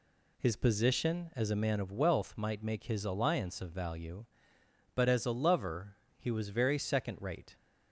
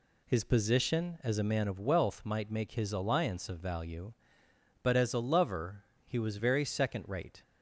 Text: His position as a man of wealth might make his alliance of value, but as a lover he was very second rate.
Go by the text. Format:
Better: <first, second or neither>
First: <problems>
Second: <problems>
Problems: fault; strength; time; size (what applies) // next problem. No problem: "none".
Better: neither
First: pauses between "lover" and "he"; slight; at 5.9 s; 0.22 s long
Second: pauses between "lover" and "he"; slight; at 5.8 s; 0.22 s long